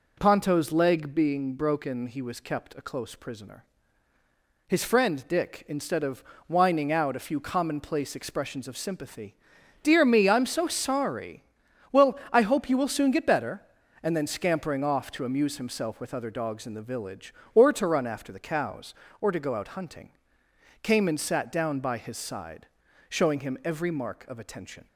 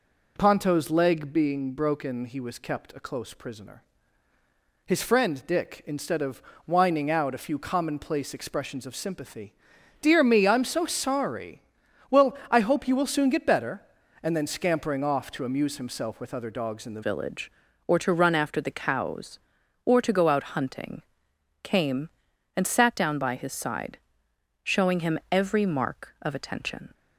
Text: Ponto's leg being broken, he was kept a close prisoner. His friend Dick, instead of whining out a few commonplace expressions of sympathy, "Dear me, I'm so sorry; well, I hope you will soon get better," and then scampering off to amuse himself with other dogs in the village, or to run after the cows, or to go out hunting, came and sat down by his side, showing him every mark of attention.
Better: first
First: pauses between "of" and "whining"; slight; at 6.2 s; 0.24 s long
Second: pauses between "of" and "whining"; slight; at 6.4 s; 0.24 s long // changes voice at "village"; from 17.0 s on; 9.9 s long

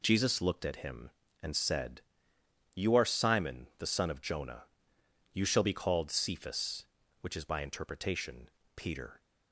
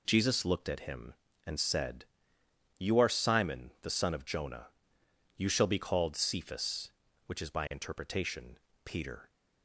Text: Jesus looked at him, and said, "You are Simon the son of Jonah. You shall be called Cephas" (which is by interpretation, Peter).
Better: neither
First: none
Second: none

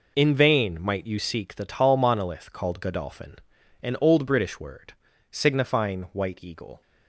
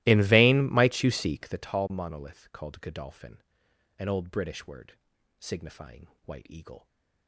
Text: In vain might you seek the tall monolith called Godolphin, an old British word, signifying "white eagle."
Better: first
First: none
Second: starts louder than the rest; strong; until 1.7 s; 17.5 dB // pauses between "signifying" and "white"; slight; at 6.0 s; 0.18 s long

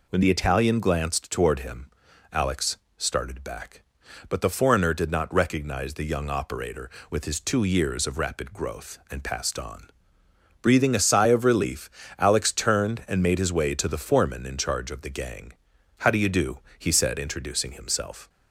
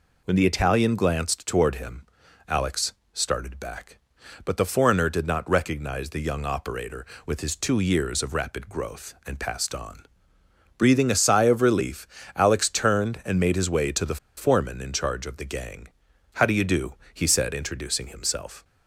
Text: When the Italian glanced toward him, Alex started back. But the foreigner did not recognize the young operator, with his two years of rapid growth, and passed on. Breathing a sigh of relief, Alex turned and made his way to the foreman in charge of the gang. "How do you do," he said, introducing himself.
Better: first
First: pauses between "Alex" and "started"; slight; at 2.7 s; 0.18 s long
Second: pauses between "Alex" and "started"; slight; at 2.9 s; 0.18 s long // pauses between "the" and "foreman"; slight; at 14.1 s; 0.21 s long

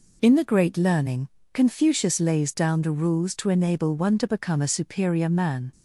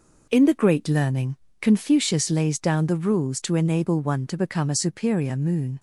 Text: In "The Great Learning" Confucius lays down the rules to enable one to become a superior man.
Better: first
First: pauses between "Learning" and "Confucius"; slight; at 1.2 s; 0.24 s long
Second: pauses between "Learning" and "Confucius"; slight; at 1.3 s; 0.24 s long // says "moon" for "man"; at 5.3 s

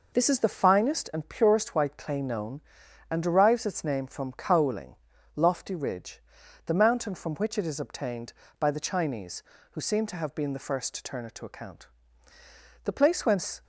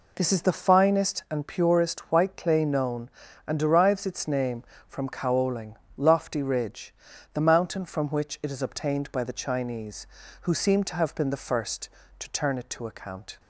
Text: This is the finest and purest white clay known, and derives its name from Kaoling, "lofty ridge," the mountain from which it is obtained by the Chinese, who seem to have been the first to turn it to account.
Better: second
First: goes on to say "The place whence"; noticeable; from 12.8 s on; 0.80 s long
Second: none

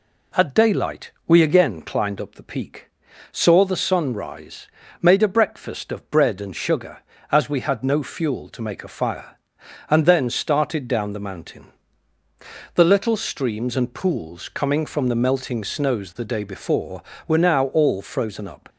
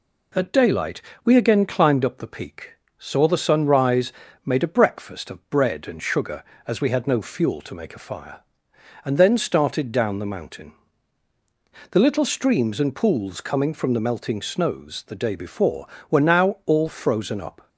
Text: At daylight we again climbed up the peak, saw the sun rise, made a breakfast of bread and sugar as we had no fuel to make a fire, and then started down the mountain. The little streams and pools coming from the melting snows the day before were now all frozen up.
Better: neither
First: pauses between "daylight" and "we"; slight; at 1.1 s; 0.16 s long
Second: pauses between "daylight" and "we"; slight; at 1.0 s; 0.22 s long

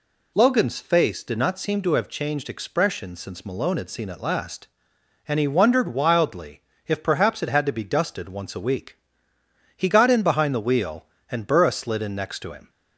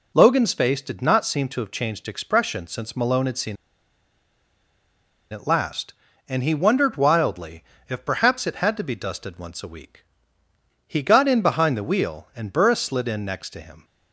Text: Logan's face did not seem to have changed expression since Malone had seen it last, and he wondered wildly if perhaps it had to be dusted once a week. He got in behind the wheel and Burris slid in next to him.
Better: first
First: pauses between "wildly" and "if"; slight; at 6.6 s; 0.26 s long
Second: pauses between "seen" and "it"; strong; at 3.5 s; 1.7 s long // pauses between "wildly" and "if"; slight; at 7.6 s; 0.28 s long

